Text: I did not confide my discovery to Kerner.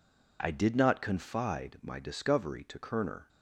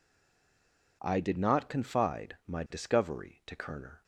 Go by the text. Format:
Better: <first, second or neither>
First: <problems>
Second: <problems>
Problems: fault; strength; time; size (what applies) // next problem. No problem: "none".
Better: first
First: none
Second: stays silent before the first word; until 1.0 s; 1.0 s long